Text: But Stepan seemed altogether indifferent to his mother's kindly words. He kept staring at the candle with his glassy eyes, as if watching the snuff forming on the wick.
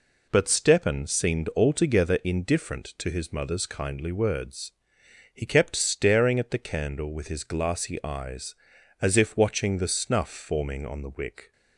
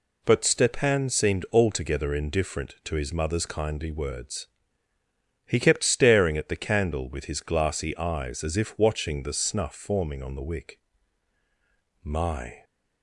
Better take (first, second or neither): first